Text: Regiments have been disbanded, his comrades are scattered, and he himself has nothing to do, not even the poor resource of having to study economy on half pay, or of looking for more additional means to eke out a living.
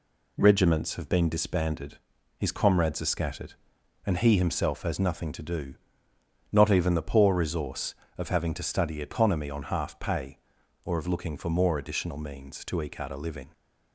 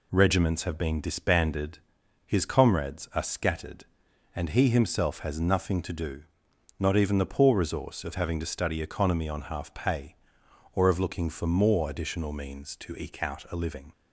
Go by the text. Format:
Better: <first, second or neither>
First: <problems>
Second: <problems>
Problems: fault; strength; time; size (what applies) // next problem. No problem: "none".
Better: neither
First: none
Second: none